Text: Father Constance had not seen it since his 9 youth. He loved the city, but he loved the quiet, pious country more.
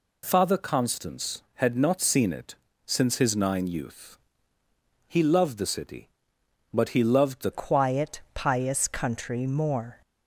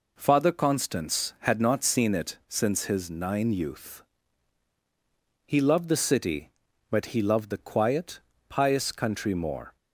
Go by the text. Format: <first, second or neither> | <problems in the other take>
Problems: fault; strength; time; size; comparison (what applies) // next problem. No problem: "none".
second | pauses between "it" and "since"; slight; at 2.5 s; 0.32 s long // changes voice at "quiet"; from 7.5 s on; 2.5 s long